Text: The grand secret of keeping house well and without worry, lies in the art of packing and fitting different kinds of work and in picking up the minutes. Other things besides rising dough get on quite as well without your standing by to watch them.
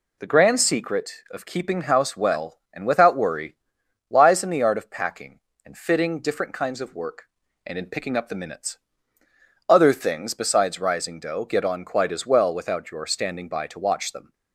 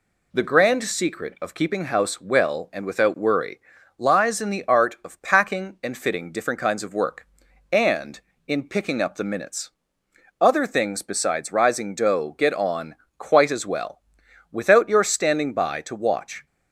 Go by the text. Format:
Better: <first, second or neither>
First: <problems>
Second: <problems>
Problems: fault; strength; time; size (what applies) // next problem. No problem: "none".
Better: first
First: none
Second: pauses between "on" and "quite"; slight; at 12.9 s; 0.22 s long // pauses between "well" and "without"; noticeable; at 13.9 s; 0.50 s long // stops before "them"; at 16.4 s